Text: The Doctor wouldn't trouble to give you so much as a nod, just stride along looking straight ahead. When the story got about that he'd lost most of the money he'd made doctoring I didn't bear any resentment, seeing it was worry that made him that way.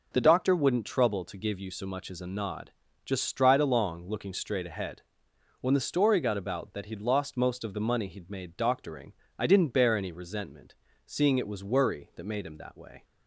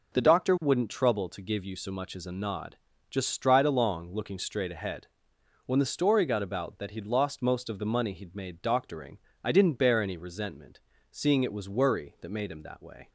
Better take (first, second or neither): neither